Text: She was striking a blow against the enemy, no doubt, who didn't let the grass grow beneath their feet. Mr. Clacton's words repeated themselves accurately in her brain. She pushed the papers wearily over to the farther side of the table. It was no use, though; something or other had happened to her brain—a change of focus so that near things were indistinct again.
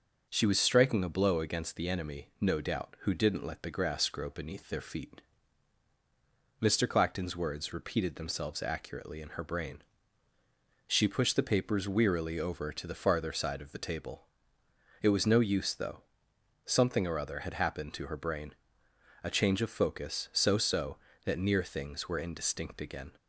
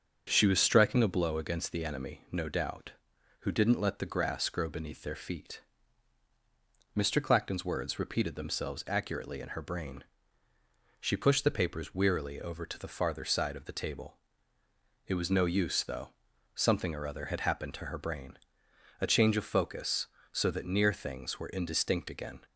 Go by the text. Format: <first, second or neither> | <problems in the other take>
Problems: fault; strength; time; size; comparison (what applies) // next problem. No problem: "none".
second | starts louder than the rest; until 1.2 s; 6.5 dB; strong in the second // says "so" twice; at 20.5 s